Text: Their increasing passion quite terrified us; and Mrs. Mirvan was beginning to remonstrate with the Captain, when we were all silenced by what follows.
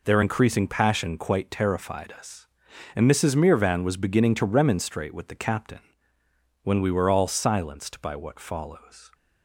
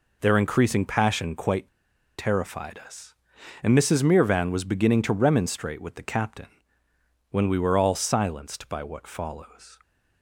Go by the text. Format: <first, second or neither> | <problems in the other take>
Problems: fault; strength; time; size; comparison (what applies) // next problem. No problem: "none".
first | pauses between "quite" and "terrified"; noticeable; at 1.6 s; 0.49 s long